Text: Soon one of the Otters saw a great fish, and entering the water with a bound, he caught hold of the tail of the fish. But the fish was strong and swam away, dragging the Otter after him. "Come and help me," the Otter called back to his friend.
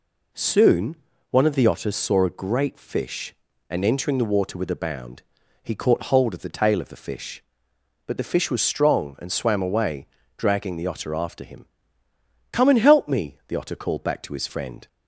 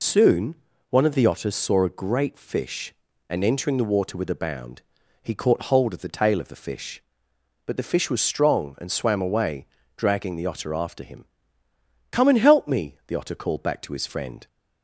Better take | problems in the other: first | loses the start of "Soon"; at 0.0 s; 85 ms // pauses between "Soon" and "one"; slight; at 0.5 s; 0.34 s long; slight in the first

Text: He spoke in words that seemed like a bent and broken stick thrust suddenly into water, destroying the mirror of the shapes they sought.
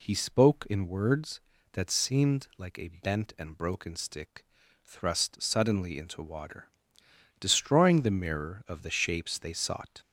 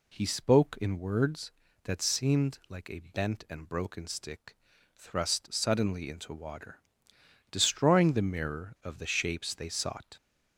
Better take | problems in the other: neither | pauses between "stick" and "thrust"; the same in both

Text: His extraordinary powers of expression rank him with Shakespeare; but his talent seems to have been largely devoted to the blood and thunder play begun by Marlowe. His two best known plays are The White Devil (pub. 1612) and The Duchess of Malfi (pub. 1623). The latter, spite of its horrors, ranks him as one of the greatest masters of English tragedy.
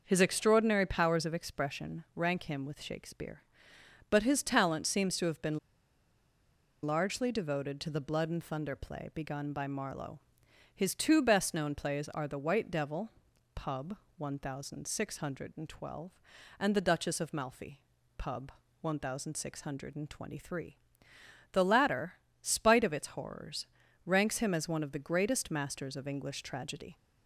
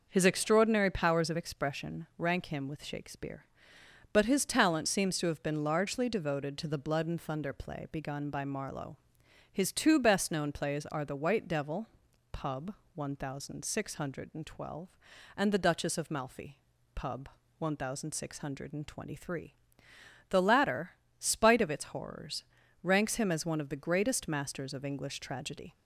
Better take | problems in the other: second | pauses between "been" and "largely"; strong; at 5.5 s; 1.2 s long

